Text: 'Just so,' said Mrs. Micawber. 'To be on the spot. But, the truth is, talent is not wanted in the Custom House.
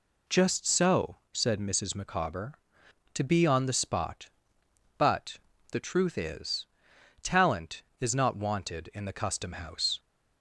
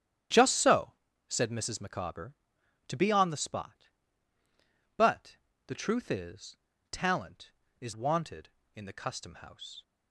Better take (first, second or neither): first